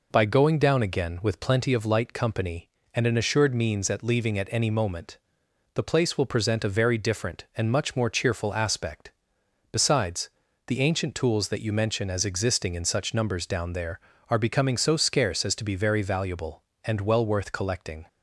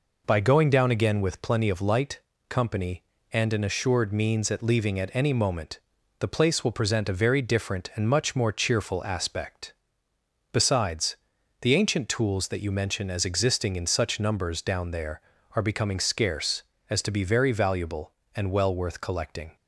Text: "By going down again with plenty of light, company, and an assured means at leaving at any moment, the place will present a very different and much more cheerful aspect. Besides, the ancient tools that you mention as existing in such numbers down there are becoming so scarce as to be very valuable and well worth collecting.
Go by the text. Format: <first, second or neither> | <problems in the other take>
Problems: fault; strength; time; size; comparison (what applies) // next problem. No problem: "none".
first | skips "so"; at 15.9 s